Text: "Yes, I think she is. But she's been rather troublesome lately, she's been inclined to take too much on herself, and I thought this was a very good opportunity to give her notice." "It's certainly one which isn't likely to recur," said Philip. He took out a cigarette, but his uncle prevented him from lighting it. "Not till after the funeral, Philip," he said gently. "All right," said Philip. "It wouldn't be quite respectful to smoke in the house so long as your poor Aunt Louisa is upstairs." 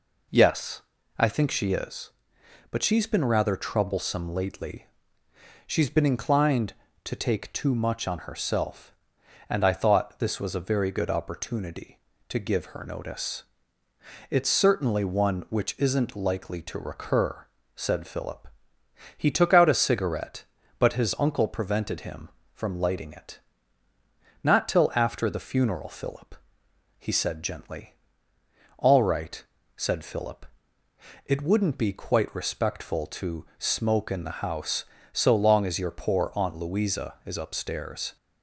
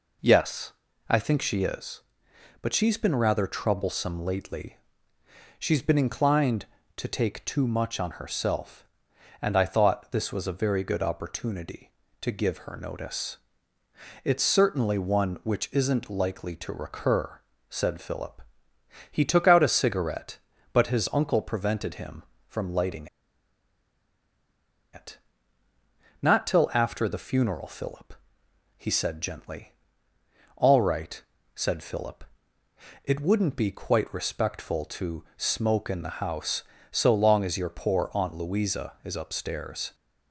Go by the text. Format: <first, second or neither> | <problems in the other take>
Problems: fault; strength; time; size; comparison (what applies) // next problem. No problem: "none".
first | pauses between "lighting" and "it"; strong; at 23.0 s; 1.8 s long